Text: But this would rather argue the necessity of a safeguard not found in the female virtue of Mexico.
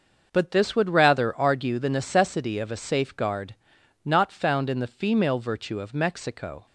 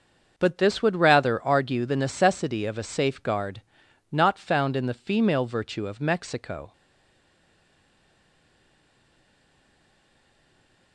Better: first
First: starts louder than the rest; until 1.3 s; 6 dB // pauses between "safeguard" and "not"; noticeable; at 3.5 s; 0.50 s long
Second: starts louder than the rest; until 1.3 s; 6 dB // pauses between "safeguard" and "not"; noticeable; at 3.6 s; 0.50 s long // stays silent after the last word; strong; from 6.7 s on; 4.2 s long

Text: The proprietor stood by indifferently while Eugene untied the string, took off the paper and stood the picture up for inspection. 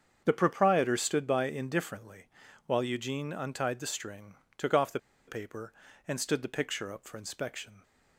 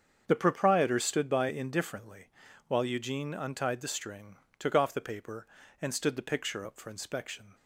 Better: second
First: starts louder than the rest; strong; until 1.2 s; 7.5 dB // pauses between "indifferently" and "while"; at 2.2 s; 0.40 s long // pauses between "the" and "paper"; slight; at 4.9 s; 0.28 s long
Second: starts louder than the rest; strong; until 1.2 s; 7.5 dB // pauses between "indifferently" and "while"; at 2.2 s; 0.40 s long

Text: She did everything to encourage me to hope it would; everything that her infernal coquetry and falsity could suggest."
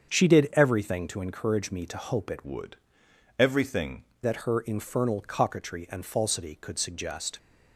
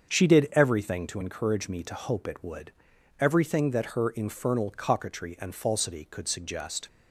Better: second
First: starts louder than the rest; strong; until 1.1 s; 7 dB // changes voice from "would" to "everything"; from 2.4 to 4.0 s; 1.6 s long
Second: starts louder than the rest; until 1.1 s; 7 dB

